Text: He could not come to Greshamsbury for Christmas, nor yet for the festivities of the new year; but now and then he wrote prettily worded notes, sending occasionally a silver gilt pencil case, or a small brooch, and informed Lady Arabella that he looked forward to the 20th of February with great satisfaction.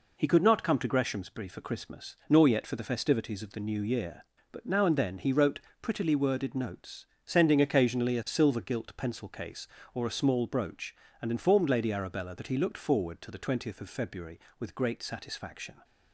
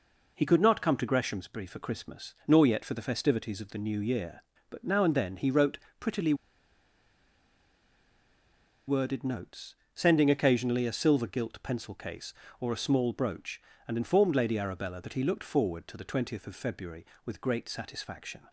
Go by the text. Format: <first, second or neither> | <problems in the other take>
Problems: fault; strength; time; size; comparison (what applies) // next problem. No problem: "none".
first | pauses between "wrote" and "prettily"; slight; at 5.7 s; 0.20 s long; slight in the first // pauses between "prettily" and "worded"; strong; at 6.3 s; 2.5 s long